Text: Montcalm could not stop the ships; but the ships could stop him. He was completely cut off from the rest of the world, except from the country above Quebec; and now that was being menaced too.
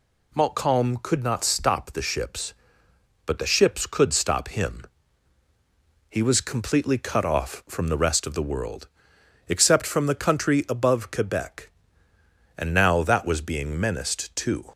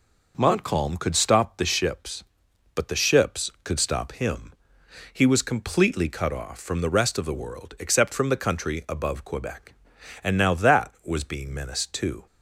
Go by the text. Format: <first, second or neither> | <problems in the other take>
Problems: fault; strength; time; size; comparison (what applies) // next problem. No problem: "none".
first | skips "not"; at 1.1 s